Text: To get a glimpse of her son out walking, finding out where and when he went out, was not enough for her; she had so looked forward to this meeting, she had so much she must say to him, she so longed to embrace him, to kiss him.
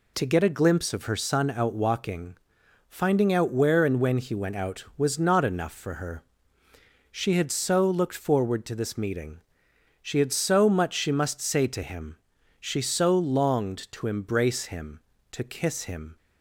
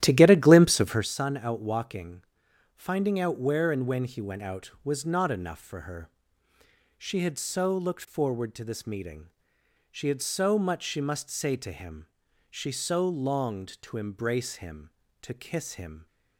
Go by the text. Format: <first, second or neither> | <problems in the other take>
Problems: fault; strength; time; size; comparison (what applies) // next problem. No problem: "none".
first | starts louder than the rest; strong; until 1.2 s; 12.5 dB